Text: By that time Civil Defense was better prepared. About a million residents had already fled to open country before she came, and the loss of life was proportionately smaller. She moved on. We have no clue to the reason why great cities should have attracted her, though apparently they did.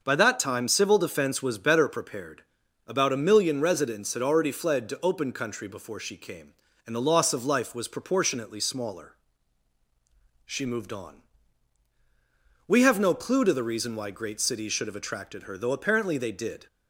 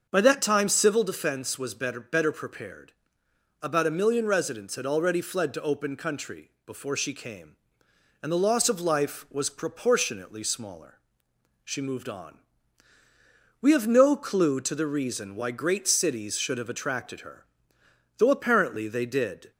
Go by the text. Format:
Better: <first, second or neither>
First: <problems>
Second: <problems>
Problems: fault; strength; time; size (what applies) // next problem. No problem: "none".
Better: first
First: starts louder than the rest; until 1.0 s; 6 dB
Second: starts louder than the rest; until 1.1 s; 6.5 dB // says "better" twice; at 1.9 s